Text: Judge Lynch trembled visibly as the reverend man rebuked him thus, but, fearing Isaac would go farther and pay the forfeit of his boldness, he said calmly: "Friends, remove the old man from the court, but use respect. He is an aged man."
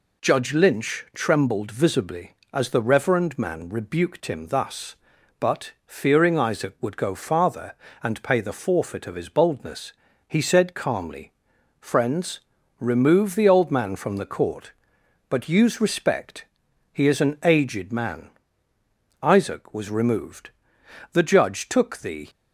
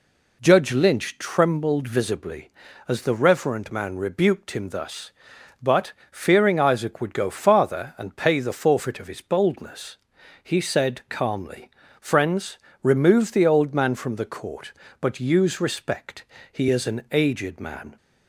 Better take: second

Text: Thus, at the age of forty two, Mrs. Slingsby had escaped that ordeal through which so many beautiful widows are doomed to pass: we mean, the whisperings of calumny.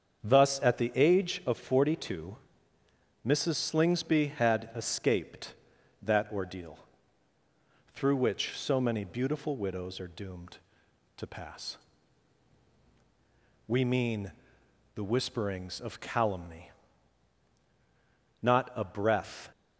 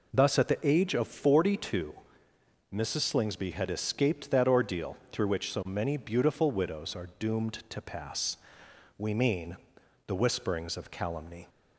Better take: second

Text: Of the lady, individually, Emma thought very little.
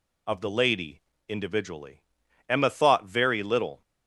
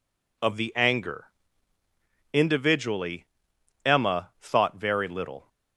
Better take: first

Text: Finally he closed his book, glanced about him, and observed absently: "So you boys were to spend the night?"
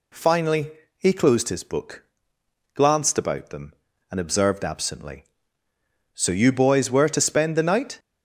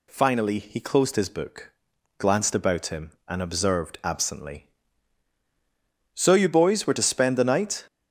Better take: second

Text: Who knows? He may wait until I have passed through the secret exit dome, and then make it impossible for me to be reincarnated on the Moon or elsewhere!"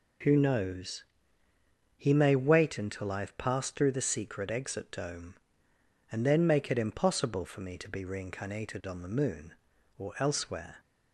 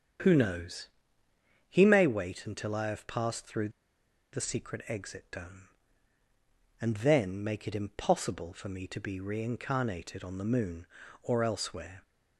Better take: first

